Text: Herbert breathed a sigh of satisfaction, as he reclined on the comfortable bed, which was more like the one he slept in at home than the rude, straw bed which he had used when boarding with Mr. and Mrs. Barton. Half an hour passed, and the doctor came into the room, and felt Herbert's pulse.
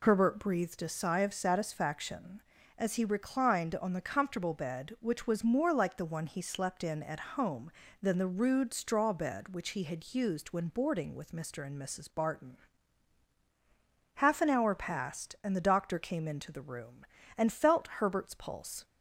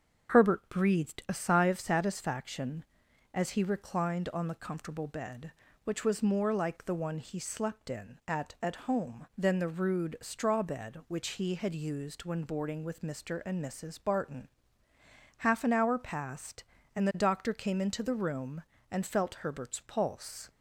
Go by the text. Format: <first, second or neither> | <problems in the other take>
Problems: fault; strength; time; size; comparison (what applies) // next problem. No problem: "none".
first | starts louder than the rest; strong; until 1.3 s; 7.5 dB // says "at" twice; at 8.6 s